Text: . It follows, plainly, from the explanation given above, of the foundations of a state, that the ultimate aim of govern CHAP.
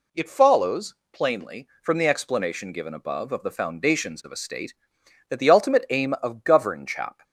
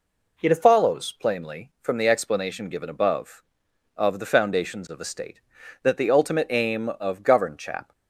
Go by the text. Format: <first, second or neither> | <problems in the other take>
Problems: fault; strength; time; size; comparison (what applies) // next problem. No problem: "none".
neither | none